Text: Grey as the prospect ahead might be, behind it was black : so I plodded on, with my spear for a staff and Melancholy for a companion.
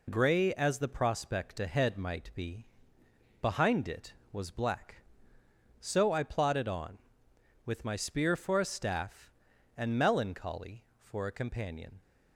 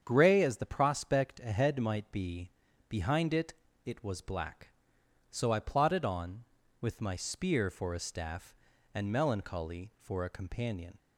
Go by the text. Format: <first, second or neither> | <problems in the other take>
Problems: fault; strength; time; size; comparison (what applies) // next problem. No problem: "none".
first | starts louder than the rest; strong; until 1.0 s; 8 dB // says "it" twice; at 3.8 s